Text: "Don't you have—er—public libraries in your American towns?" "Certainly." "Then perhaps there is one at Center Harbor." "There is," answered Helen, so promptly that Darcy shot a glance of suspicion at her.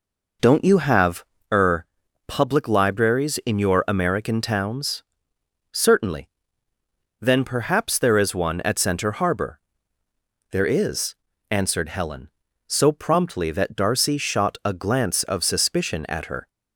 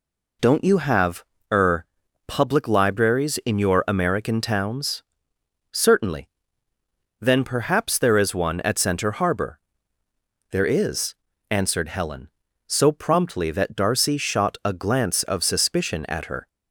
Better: second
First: starts louder than the rest; noticeable; until 1.7 s; 4.5 dB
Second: none

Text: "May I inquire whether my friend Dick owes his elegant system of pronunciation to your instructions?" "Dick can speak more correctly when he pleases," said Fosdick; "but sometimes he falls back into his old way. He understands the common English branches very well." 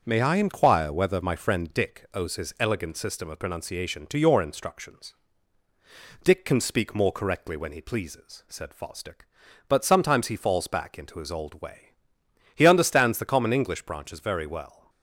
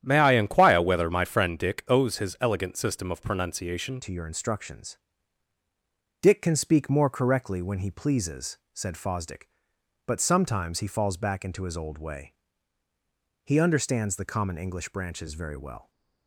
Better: first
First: starts louder than the rest; until 1.0 s; 6.5 dB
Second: starts louder than the rest; strong; until 1.0 s; 10.5 dB // changes voice at "to"; from 4.0 s on; 11.9 s long

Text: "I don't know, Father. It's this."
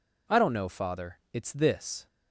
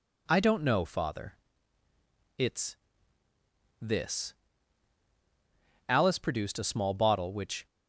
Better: first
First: none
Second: pauses between "It's" and "this"; at 2.7 s; 1.0 s long // goes on to say "Alice produced a small bottle which"; strong; from 5.8 s on; 1.7 s long

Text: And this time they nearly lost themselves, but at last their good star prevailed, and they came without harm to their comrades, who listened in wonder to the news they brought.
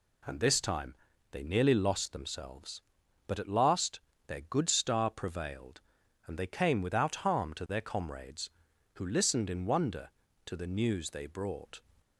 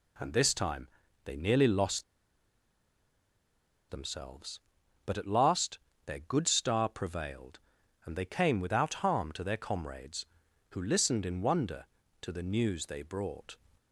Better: first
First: pauses between "time" and "they"; at 0.9 s; 0.38 s long // pauses between "last" and "their"; slight; at 3.9 s; 0.28 s long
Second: pauses between "time" and "they"; at 0.8 s; 0.38 s long // pauses between "lost" and "themselves"; strong; at 2.0 s; 1.8 s long // pauses between "last" and "their"; slight; at 5.7 s; 0.28 s long

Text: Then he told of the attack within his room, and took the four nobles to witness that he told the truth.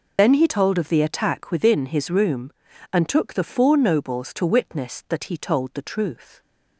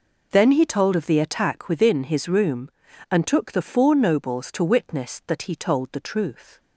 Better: second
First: loses the start of "Then"; at 0.1 s; 55 ms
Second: none

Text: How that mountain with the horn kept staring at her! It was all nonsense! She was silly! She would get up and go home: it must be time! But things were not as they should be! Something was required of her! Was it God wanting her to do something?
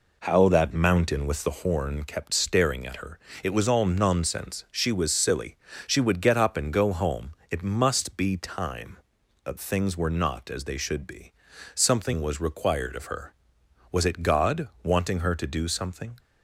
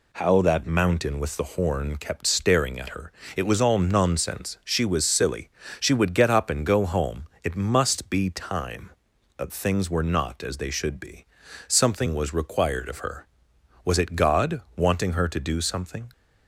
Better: second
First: starts louder than the rest; until 1.8 s; 3.5 dB // pauses between "God" and "wanting"; slight; at 14.6 s; 0.16 s long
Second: pauses between "God" and "wanting"; slight; at 14.5 s; 0.16 s long

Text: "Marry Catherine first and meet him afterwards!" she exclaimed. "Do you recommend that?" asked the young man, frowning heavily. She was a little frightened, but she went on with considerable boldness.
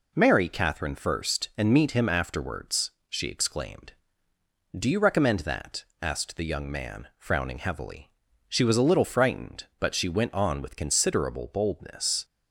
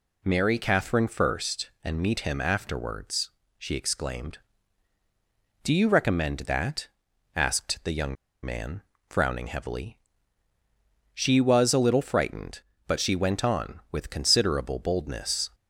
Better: first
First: none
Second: pauses between "young" and "man"; slight; at 8.1 s; 0.29 s long

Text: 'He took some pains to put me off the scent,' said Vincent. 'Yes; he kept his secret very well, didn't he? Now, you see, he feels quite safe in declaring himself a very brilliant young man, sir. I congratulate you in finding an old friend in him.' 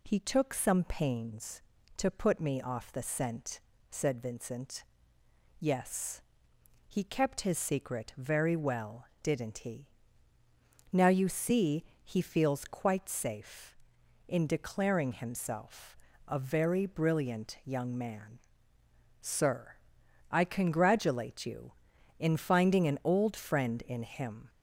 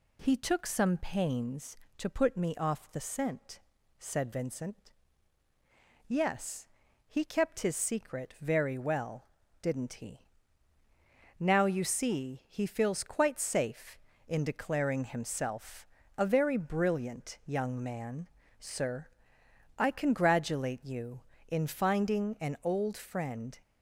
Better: first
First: pauses between "himself" and "a"; slight; at 15.9 s; 0.30 s long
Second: pauses between "himself" and "a"; slight; at 15.8 s; 0.32 s long // stops before "in him"; at 23.6 s

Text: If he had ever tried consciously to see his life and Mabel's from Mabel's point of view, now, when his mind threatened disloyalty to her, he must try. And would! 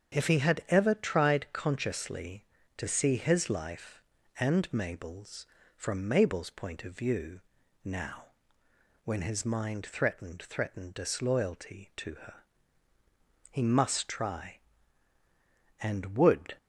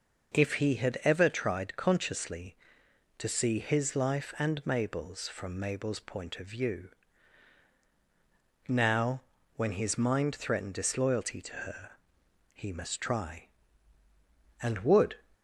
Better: second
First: starts louder than the rest; strong; until 1.2 s; 7.5 dB // says "threatened" twice; at 10.4 s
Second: none

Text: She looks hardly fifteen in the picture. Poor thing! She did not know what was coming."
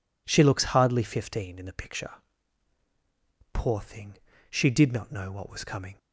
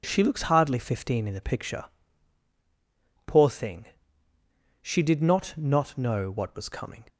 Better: first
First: none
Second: says "not" twice; at 5.5 s

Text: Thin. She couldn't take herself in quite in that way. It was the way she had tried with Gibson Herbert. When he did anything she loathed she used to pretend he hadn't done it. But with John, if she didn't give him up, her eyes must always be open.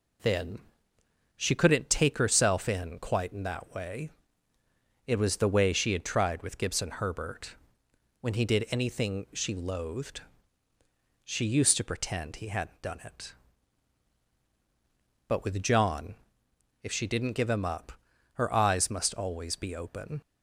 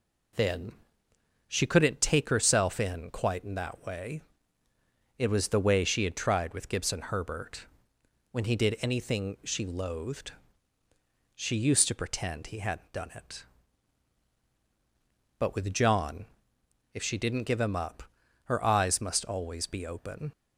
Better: neither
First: pauses between "loathed" and "she"; at 10.2 s; 1.0 s long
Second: pauses between "loathed" and "she"; at 10.3 s; 1.0 s long

